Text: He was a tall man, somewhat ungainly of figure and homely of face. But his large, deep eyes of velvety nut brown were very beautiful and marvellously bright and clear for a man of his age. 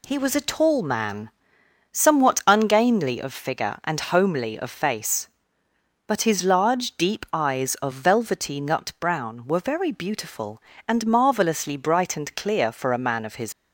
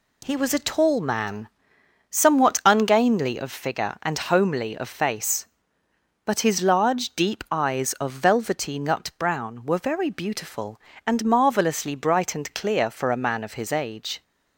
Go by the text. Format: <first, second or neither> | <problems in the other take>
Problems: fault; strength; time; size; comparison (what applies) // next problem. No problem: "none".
second | stops before "age"; at 13.5 s